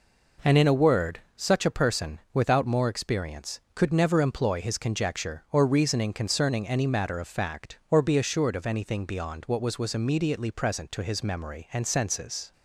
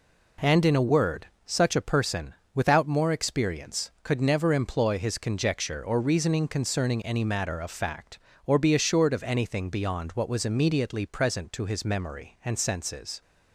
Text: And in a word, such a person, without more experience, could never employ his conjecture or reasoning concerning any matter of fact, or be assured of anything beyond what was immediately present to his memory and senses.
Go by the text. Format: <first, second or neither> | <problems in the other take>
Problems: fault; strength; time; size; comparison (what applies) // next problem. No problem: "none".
second | says "was" twice; at 9.7 s